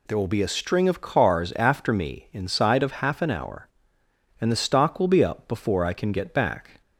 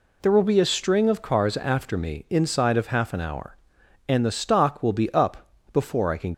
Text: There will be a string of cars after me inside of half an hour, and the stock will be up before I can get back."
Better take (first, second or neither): first